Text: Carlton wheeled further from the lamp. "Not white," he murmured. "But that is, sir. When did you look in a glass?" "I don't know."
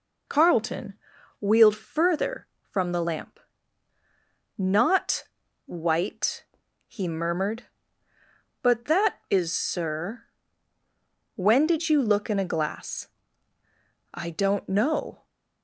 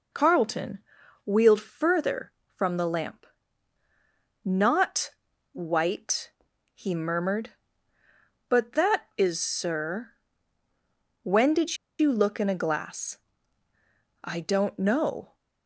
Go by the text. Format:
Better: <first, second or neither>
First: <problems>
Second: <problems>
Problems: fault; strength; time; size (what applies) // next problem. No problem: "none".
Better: first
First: pauses between "Carlton" and "wheeled"; noticeable; at 0.9 s; 0.46 s long // pauses between "Not" and "white"; at 5.2 s; 0.42 s long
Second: pauses between "Carlton" and "wheeled"; noticeable; at 0.7 s; 0.46 s long // pauses between "Not" and "white"; at 5.1 s; 0.42 s long // pauses between "did" and "you"; slight; at 11.7 s; 0.23 s long